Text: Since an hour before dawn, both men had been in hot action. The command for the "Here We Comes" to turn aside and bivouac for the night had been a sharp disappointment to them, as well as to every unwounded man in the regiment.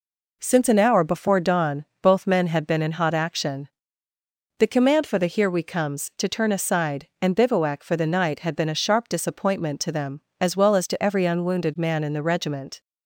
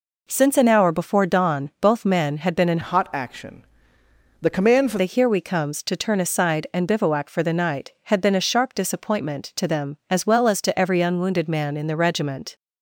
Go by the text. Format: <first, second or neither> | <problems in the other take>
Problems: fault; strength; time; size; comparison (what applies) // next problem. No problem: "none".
first | changes voice from "hot" to "for"; from 2.8 to 4.9 s; 2.1 s long